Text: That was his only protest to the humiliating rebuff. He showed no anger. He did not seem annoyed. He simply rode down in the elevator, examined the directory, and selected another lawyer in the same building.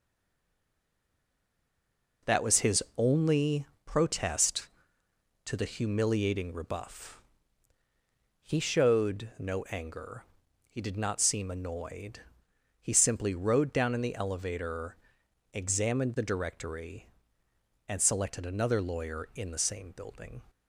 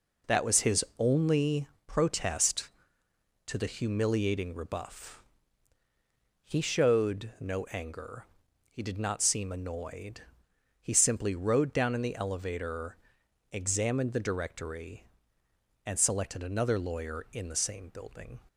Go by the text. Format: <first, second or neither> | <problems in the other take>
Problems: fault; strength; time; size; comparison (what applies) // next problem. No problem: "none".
second | stays silent before the first word; until 2.2 s; 2.2 s long // pauses between "only" and "protest"; slight; at 3.6 s; 0.20 s long; slight in the second